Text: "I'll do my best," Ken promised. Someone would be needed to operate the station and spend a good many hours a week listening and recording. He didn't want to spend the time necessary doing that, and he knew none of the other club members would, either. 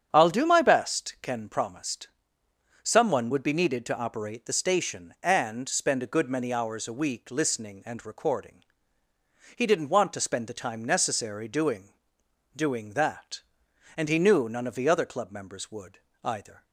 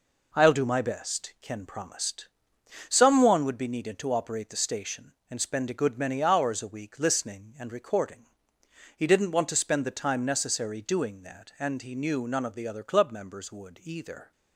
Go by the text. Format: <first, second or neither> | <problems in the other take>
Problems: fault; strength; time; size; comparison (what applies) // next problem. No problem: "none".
second | starts louder than the rest; strong; until 1.1 s; 8 dB // says "doing" twice; at 12.5 s